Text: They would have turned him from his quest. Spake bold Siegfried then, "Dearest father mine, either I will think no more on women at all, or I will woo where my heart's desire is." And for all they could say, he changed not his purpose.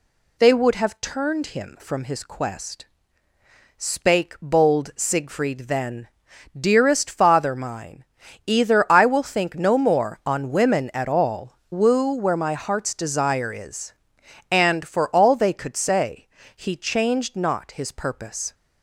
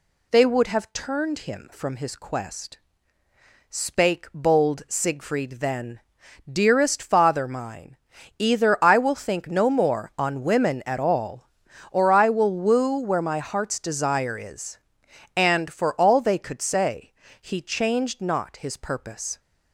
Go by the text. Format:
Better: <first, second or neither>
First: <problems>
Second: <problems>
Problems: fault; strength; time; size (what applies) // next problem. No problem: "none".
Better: second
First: skips "or I will"; at 11.6 s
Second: none